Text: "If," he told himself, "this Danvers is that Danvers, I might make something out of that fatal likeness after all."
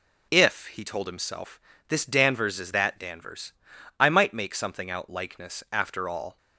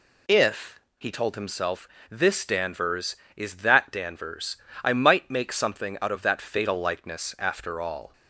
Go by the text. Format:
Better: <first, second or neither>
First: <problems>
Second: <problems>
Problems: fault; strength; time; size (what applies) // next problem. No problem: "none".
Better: second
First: skips "of that fatal"; at 5.0 s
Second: none